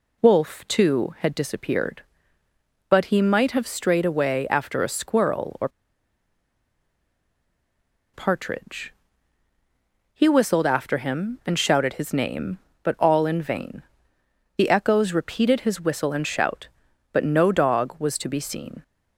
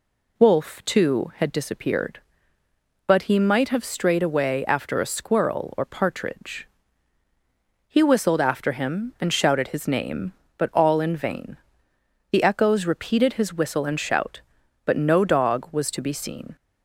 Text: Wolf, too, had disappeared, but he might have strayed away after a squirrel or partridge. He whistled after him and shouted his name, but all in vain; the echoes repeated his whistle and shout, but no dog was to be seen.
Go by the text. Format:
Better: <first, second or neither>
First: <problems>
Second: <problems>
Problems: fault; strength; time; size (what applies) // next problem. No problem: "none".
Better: second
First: pauses between "or" and "partridge"; strong; at 5.6 s; 2.4 s long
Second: none